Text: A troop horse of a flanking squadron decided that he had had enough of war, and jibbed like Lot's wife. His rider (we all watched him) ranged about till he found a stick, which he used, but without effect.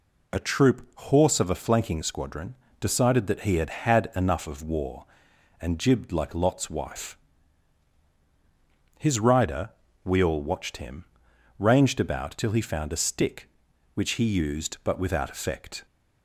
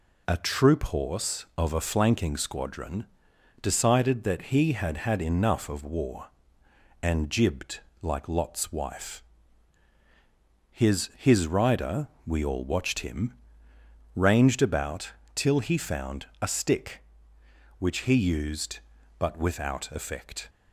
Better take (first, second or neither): first